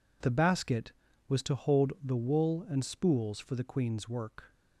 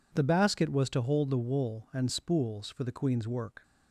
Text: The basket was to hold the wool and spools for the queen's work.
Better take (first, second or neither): neither